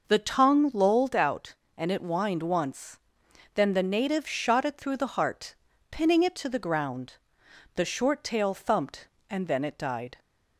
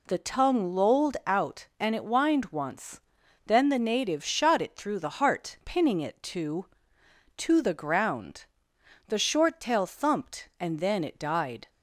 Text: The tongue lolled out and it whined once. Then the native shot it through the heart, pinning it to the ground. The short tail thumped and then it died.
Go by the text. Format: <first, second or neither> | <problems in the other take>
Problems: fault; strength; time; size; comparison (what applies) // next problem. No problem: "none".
first | says "to" twice; at 7.3 s